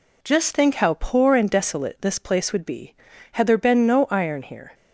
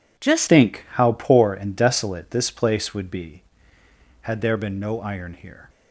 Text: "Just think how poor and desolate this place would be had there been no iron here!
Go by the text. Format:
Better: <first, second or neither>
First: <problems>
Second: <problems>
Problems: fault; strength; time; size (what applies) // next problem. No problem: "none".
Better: first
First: none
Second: changes voice at "think"; from 0.4 s on; 5.2 s long